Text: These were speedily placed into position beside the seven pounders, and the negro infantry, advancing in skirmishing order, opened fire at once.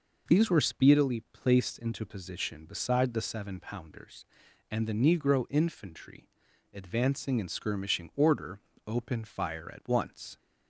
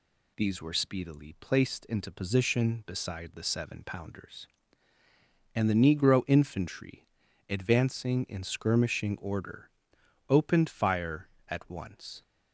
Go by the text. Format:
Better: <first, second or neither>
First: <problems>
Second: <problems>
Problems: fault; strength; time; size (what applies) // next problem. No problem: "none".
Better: neither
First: none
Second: none